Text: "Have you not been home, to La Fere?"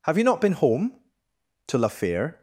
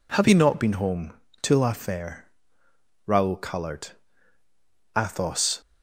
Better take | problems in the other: first | goes on to say "Raoul colored Athos"; strong; from 3.0 s on; 2.5 s long

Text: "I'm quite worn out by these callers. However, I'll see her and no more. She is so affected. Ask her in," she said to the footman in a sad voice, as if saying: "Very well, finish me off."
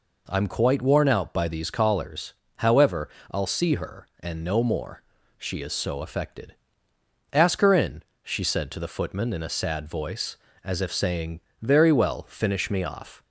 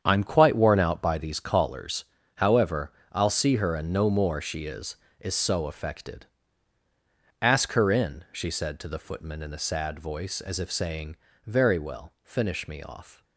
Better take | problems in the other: first | starts louder than the rest; strong; until 1.0 s; 8 dB // says "is" twice; at 5.1 s

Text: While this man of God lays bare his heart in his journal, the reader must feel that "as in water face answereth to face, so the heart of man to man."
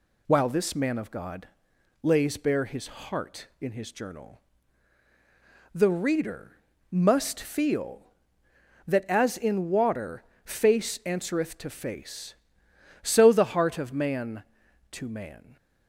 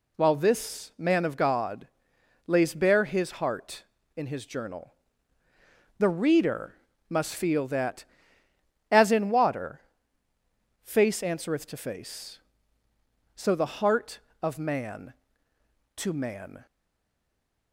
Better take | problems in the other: first | pauses between "God" and "lays"; noticeable; at 1.8 s; 0.60 s long; noticeable in the first // pauses between "reader" and "must"; slight; at 6.7 s; 0.36 s long; slight in the first // pauses between "water" and "face"; at 9.8 s; 1.0 s long; slight in the first // stays silent after the last word; from 16.6 s on; 1.1 s long

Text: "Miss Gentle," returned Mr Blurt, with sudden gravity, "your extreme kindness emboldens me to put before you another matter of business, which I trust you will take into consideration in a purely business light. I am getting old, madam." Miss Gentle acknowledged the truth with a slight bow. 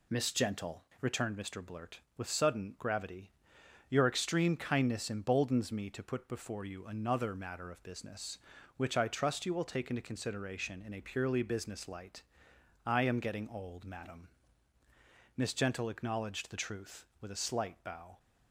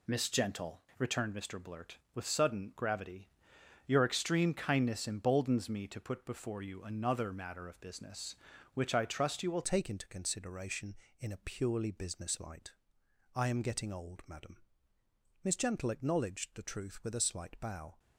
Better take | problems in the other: first | changes voice at "take"; from 9.6 s on; 8.3 s long

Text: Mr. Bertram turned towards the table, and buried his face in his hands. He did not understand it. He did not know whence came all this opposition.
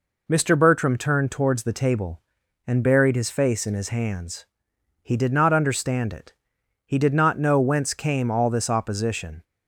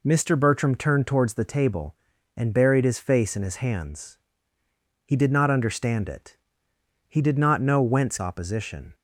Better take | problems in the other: first | skips "came all this"; at 8.1 s

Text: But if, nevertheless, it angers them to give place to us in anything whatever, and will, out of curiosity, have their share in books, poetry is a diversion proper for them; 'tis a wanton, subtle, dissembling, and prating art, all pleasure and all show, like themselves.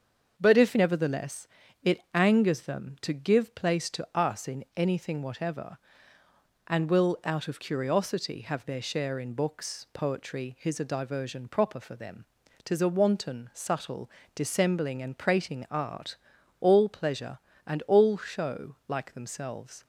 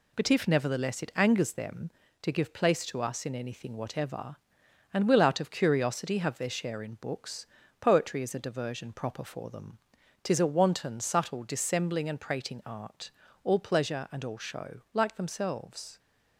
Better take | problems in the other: second | starts louder than the rest; until 1.3 s; 6.5 dB // says "his" for "is"; at 10.5 s

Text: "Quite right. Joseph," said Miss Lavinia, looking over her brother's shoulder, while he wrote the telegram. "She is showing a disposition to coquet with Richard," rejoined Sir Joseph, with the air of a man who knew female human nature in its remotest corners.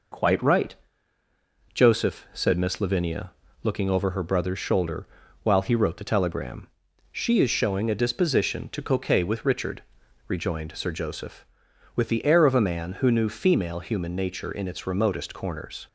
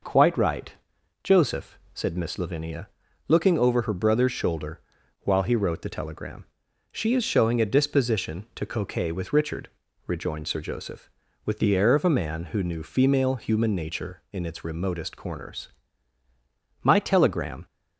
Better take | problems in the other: first | goes on to say "My telegram"; noticeable; from 16.8 s on; 0.82 s long

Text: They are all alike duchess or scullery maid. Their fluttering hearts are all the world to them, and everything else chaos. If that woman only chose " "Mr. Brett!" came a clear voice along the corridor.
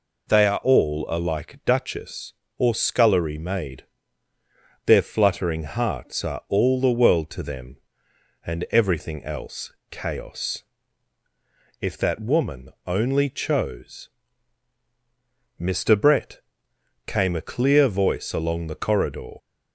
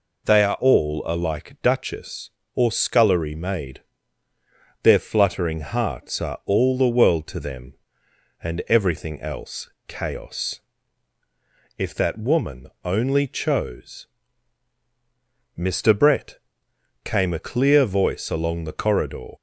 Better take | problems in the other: neither | pauses between "else" and "chaos"; slight; the same in both // pauses between "woman" and "only"; slight; the same in both

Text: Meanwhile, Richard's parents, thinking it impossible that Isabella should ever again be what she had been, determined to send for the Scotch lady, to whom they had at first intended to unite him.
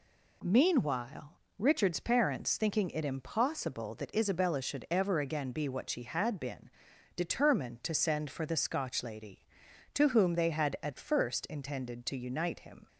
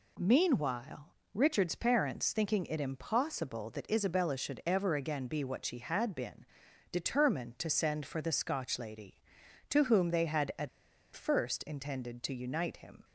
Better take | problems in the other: first | pauses between "at" and "first"; noticeable; at 10.6 s; 0.46 s long

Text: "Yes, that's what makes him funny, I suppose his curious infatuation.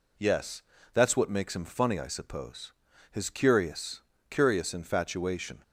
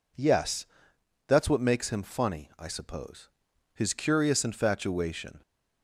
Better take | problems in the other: second | pauses between "suppose" and "his"; at 2.7 s; 0.38 s long; noticeable in the second // says "curious" twice; at 4.2 s

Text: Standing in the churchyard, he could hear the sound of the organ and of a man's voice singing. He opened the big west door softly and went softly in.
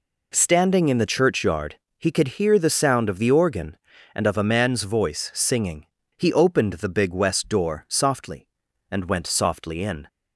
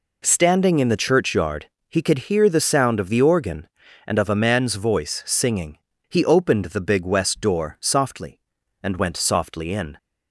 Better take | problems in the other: neither | none

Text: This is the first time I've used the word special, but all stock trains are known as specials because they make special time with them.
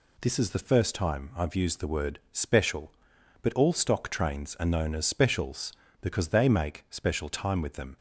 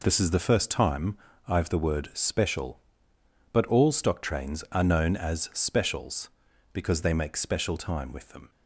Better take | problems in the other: first | pauses between "time" and "I've"; slight; at 1.1 s; 0.30 s long // skips "used"; at 1.6 s

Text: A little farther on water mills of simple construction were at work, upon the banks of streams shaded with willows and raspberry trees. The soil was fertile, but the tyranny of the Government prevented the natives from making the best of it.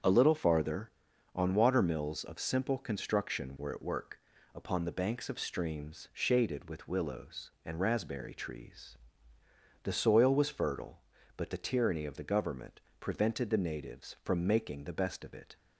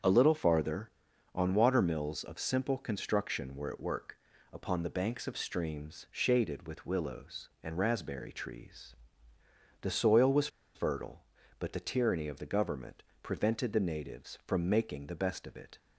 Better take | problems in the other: first | starts louder than the rest; strong; until 1.5 s; 7.5 dB; strong in the first // pauses between "was" and "fertile"; slight; at 10.4 s; 0.27 s long // pauses between "Government" and "prevented"; slight; at 13.0 s; 0.18 s long; slight in the first

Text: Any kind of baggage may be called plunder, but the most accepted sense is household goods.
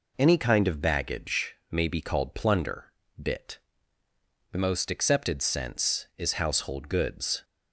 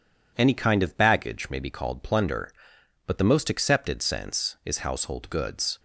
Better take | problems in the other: second | pauses between "baggage" and "may"; slight; at 1.5 s; 0.16 s long // says "bit" for "but"; at 3.1 s

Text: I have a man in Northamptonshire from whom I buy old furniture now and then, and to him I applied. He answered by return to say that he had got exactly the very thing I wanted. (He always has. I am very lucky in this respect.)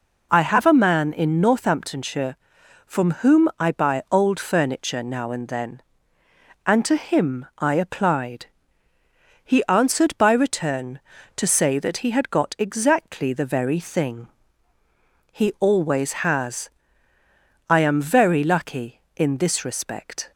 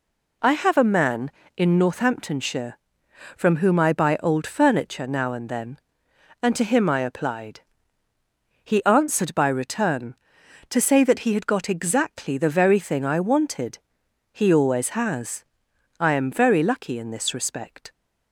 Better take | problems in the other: second | skips "I wanted"; at 14.7 s

